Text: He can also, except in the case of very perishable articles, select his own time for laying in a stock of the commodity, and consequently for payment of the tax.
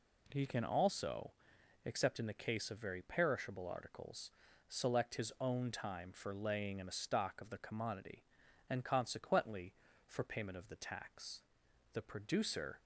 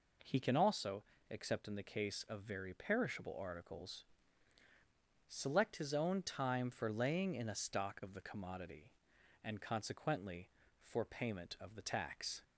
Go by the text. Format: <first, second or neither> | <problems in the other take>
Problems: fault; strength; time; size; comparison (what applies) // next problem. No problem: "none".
second | goes on to say "The producer"; noticeable; from 11.9 s on; 0.86 s long